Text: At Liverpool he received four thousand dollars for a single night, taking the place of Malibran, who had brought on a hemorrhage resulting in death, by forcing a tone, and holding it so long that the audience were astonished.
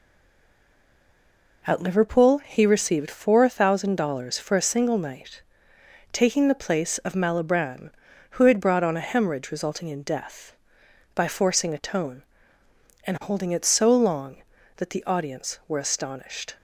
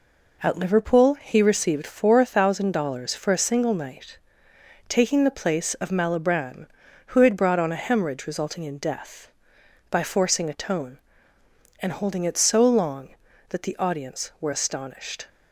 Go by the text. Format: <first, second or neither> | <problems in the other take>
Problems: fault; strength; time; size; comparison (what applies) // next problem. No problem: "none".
second | stays silent before the first word; noticeable; until 1.6 s; 1.6 s long